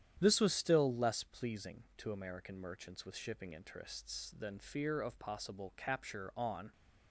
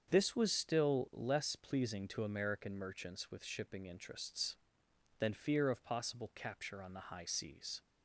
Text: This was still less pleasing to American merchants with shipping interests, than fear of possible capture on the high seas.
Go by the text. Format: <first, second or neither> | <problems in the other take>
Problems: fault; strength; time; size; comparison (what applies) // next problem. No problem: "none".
second | starts louder than the rest; strong; until 1.2 s; 10 dB; strong in the second // stops before "the high seas"; at 6.7 s